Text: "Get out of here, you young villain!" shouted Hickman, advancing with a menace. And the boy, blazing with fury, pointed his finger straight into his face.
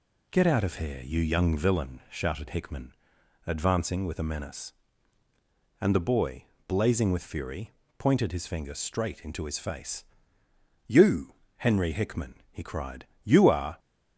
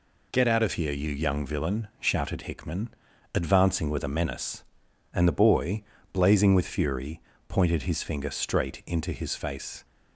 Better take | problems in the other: second | goes on to say "You Henry Hickman he cried You are"; strong; from 10.8 s on; 2.9 s long

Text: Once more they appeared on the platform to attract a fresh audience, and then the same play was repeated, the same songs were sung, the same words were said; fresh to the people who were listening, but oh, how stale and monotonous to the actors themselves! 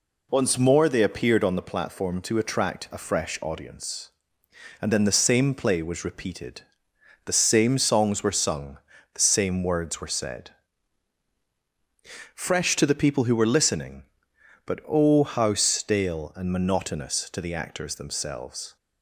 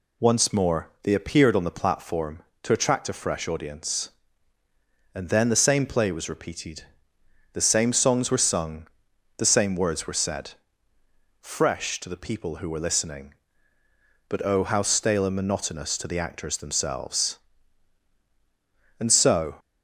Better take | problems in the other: first | goes on to say "And so"; from 18.9 s on; 0.58 s long

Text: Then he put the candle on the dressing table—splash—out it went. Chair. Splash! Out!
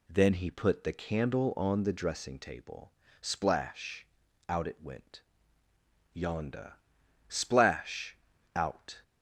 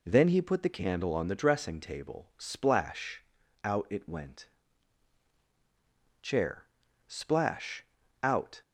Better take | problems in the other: second | says "Yonda" for "Chair"; at 6.1 s

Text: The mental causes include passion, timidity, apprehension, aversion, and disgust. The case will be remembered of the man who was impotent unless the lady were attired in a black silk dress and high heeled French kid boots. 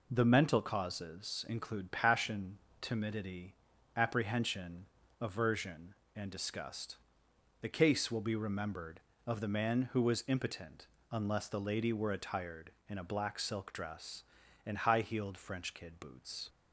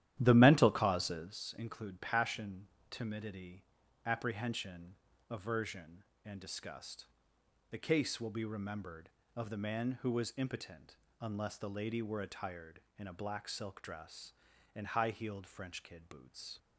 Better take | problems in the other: first | starts louder than the rest; strong; until 1.4 s; 12.5 dB // pauses between "impotent" and "unless"; slight; at 10.9 s; 0.24 s long; slight in the first

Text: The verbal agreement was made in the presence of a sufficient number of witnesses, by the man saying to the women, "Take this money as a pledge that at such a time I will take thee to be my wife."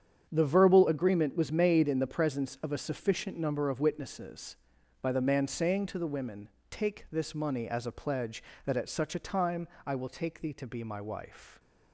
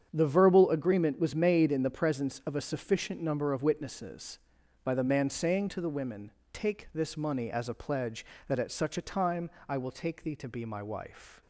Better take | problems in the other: neither | starts louder than the rest; strong; the same in both // pauses between "time" and "I"; slight; the same in both

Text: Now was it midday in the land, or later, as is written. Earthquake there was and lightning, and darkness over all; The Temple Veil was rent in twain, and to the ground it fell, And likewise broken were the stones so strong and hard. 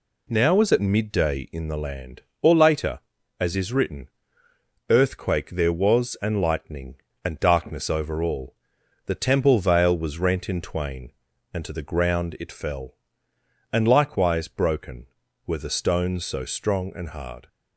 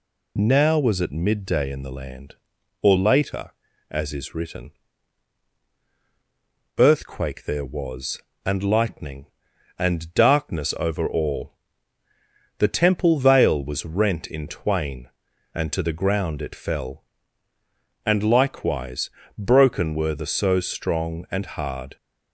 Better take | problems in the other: first | pauses between "likewise" and "broken"; slight; at 19.0 s; 0.30 s long // skips "stones"; at 20.2 s

